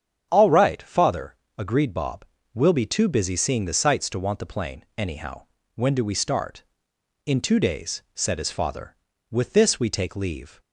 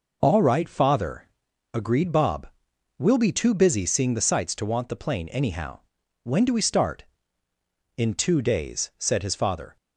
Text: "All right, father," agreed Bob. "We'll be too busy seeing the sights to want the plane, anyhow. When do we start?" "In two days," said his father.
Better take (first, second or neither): second